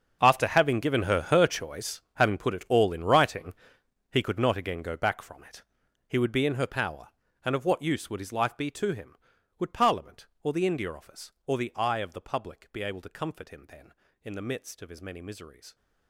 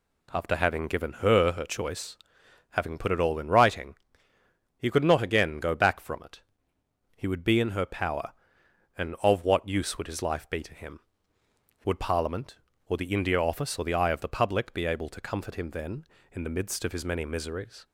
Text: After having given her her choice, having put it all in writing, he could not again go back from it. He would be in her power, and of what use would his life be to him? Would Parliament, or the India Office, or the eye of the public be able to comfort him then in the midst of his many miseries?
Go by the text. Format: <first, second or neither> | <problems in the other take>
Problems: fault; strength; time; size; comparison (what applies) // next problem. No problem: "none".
second | gets quieter; strong; throughout; 17 dB